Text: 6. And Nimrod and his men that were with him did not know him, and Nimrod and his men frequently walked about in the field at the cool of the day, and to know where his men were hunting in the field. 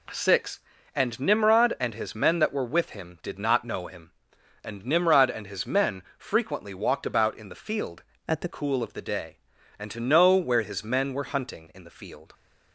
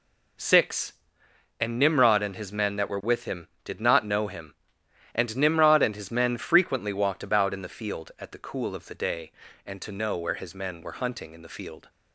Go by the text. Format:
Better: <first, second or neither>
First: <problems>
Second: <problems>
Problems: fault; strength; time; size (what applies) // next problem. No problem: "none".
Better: second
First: changes voice from "at" to "the"; from 8.2 to 8.4 s; 0.2 s long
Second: none